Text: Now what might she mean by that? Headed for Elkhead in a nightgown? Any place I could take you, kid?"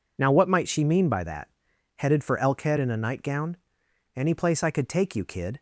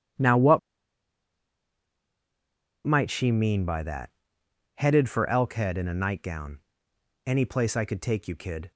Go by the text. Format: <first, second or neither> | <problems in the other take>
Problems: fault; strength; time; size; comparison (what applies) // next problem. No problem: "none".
first | pauses between "what" and "might"; strong; at 0.5 s; 2.2 s long